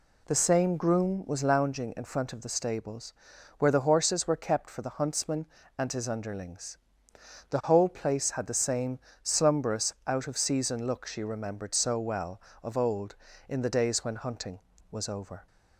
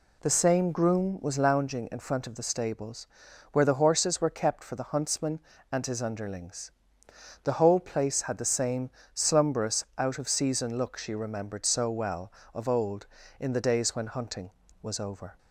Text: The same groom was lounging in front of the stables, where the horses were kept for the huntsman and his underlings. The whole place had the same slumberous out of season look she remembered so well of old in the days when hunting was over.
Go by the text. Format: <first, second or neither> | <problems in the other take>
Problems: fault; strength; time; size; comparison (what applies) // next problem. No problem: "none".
neither | pauses between "same" and "slumberous"; slight; the same in both